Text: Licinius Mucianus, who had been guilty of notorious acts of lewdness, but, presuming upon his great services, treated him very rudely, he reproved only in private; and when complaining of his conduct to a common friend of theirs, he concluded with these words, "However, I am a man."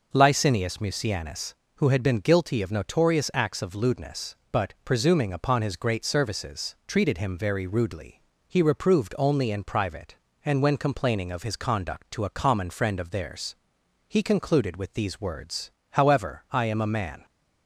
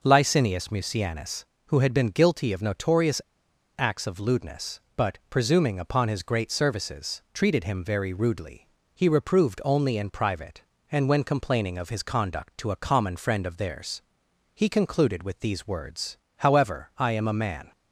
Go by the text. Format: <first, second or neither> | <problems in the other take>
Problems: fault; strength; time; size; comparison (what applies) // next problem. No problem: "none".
first | pauses between "notorious" and "acts"; noticeable; at 3.2 s; 0.56 s long